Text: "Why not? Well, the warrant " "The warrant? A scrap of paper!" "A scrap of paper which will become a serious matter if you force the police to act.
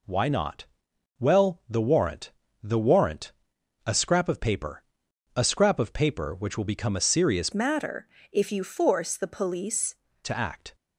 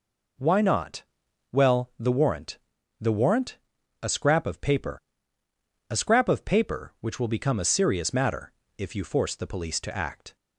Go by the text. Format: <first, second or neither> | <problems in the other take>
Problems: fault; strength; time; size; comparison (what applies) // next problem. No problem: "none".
second | changes voice from "matter" to "police"; from 7.5 to 9.9 s; 2.4 s long // pauses between "matter" and "if"; slight; at 8.0 s; 0.26 s long; slight in the second